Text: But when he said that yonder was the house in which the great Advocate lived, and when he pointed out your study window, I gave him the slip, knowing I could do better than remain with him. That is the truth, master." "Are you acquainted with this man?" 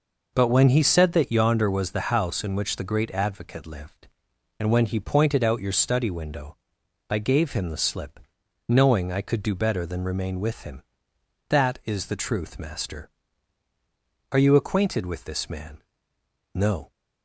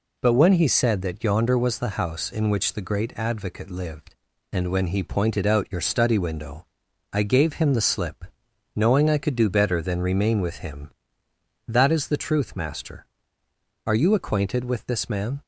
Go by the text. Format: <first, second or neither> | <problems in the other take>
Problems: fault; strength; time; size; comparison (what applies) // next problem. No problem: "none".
second | goes on to say "No"; slight; from 16.5 s on; 0.38 s long